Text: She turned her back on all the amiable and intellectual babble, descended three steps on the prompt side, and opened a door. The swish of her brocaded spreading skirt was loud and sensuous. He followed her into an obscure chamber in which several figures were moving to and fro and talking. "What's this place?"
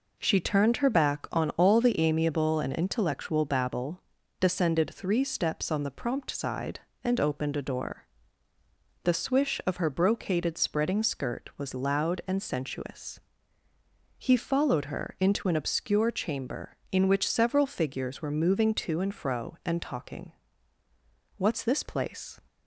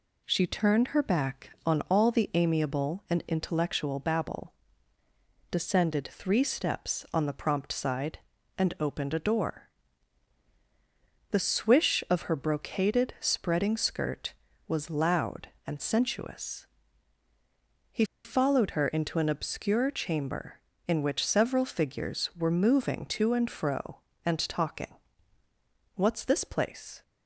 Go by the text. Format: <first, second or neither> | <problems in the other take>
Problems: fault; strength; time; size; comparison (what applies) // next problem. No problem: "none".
first | pauses between "He" and "followed"; slight; at 18.0 s; 0.21 s long